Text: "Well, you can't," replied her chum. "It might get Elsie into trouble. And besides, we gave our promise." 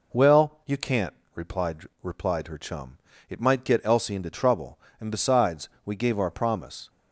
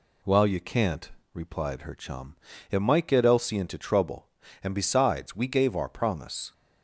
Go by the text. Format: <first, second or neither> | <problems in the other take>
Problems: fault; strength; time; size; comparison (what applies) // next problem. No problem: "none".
second | says "replied" twice; at 2.0 s